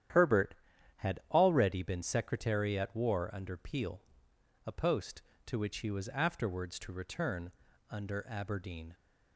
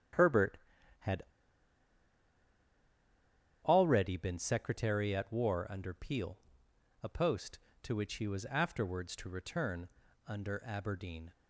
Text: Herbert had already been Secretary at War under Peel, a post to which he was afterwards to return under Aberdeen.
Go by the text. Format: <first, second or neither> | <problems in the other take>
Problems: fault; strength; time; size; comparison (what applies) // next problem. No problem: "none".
first | starts louder than the rest; strong; until 3.9 s; 10.5 dB; strong in the first // pauses between "had" and "already"; strong; at 1.2 s; 2.4 s long // pauses between "return" and "under"; at 9.8 s; 0.40 s long; also in the first